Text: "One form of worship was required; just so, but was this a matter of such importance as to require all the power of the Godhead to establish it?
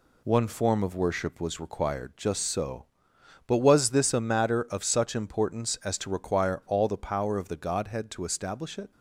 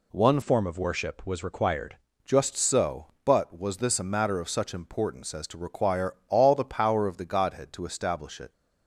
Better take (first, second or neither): first